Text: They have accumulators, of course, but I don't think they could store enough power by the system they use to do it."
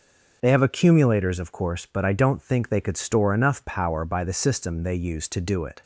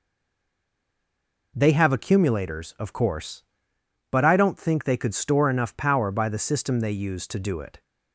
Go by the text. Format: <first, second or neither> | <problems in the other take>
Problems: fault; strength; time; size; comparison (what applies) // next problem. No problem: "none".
first | stays silent before the first word; noticeable; until 1.5 s; 1.5 s long